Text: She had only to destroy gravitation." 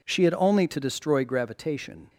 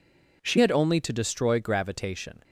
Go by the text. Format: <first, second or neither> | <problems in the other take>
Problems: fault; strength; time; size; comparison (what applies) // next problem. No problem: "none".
first | changes voice at "had"; from 0.5 s on; 1.9 s long